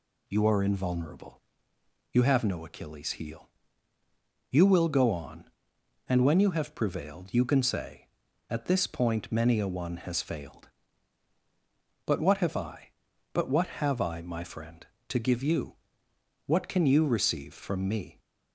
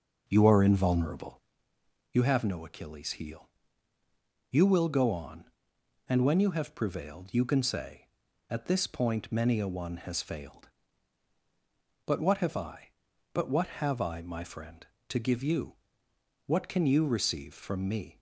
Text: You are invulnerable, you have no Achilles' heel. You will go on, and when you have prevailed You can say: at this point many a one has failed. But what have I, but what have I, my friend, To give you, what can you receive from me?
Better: first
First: none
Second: starts louder than the rest; noticeable; until 1.5 s; 5.5 dB

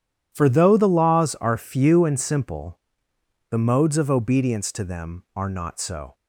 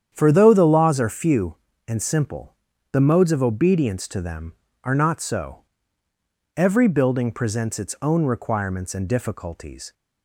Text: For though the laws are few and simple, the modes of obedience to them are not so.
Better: first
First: none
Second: starts louder than the rest; strong; until 1.1 s; 9 dB // goes on to say "Every building presents its own requirements and difficulties"; strong; from 6.5 s on; 3.3 s long

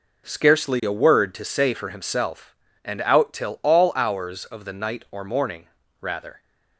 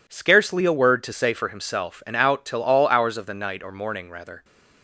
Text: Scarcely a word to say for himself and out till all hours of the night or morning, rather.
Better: neither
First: none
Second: none

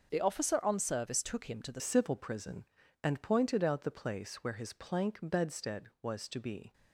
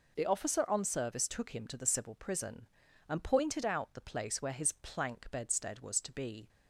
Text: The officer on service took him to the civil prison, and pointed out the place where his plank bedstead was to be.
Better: second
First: starts louder than the rest; noticeable; until 1.1 s; 6 dB // changes voice at "civil"; from 1.7 s on; 5.0 s long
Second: none

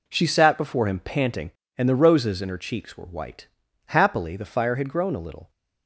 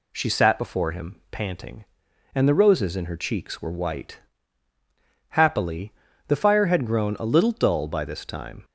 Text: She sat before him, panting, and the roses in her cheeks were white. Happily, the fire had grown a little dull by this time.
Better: second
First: stops before "dull by this time"; at 5.4 s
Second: none

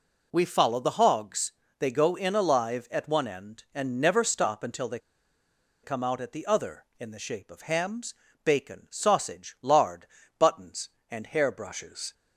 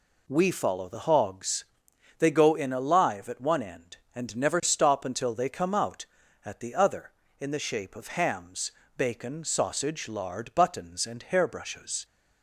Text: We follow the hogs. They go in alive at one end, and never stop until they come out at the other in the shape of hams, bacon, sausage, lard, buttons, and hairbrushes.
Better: second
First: pauses between "they" and "come"; noticeable; at 4.9 s; 0.85 s long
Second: none

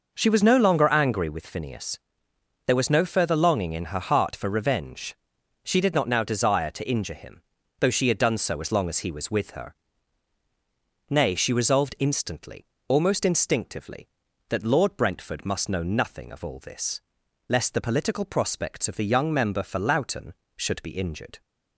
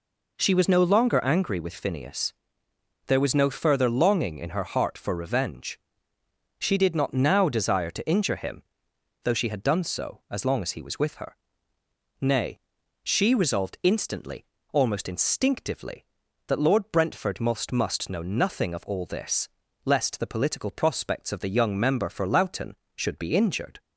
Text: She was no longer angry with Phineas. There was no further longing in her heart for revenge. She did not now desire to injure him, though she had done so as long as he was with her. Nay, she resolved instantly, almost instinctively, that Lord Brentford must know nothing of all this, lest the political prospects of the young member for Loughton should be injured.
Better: first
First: none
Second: says "must" twice; at 17.7 s

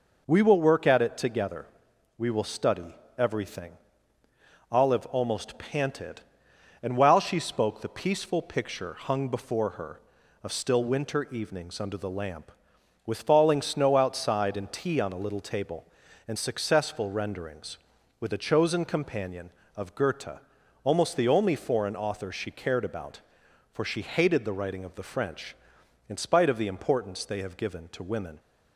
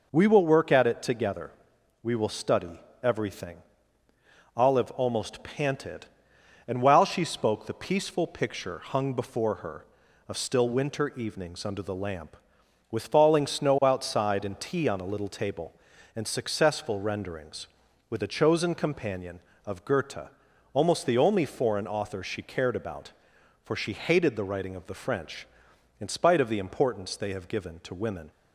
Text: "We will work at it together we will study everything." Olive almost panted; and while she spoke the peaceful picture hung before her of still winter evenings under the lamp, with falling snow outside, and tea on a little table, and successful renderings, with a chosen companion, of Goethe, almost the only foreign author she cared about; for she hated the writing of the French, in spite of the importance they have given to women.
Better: neither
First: pauses between "together" and "we"; noticeable; at 1.6 s; 0.52 s long // pauses between "study" and "everything"; slight; at 2.9 s; 0.22 s long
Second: pauses between "together" and "we"; noticeable; at 1.5 s; 0.52 s long // pauses between "study" and "everything"; slight; at 2.7 s; 0.22 s long

